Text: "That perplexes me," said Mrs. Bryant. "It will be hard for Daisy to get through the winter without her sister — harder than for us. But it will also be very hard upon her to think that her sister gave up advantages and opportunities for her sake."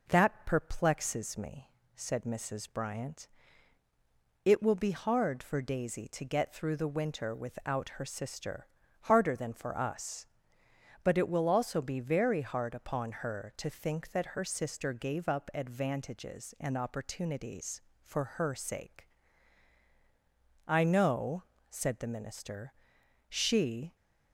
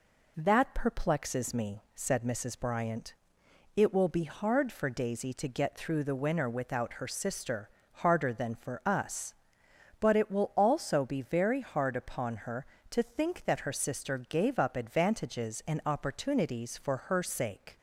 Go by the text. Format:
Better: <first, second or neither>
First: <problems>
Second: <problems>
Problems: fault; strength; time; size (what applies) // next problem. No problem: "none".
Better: second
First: goes on to say "I know said the minister she"; strong; from 20.6 s on; 3.2 s long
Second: none